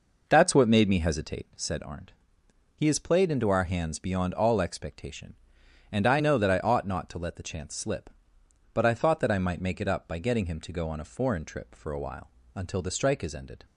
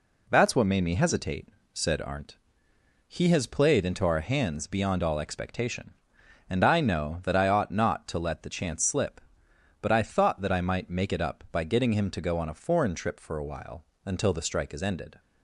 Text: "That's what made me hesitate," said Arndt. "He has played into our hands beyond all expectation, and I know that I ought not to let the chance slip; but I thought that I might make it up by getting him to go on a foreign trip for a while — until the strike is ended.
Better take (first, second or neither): second